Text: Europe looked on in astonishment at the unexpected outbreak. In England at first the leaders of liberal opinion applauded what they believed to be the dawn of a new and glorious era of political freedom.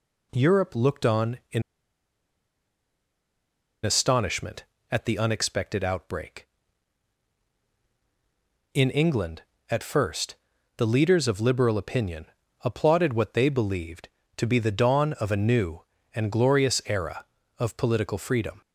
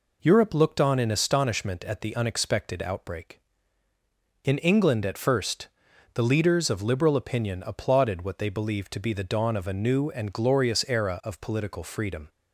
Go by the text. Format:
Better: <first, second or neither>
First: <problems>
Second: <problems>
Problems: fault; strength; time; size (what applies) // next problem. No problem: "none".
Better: second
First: pauses between "in" and "astonishment"; strong; at 1.6 s; 2.2 s long // pauses between "first" and "the"; at 10.3 s; 0.40 s long // pauses between "opinion" and "applauded"; at 12.2 s; 0.38 s long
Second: pauses between "first" and "the"; noticeable; at 5.6 s; 0.46 s long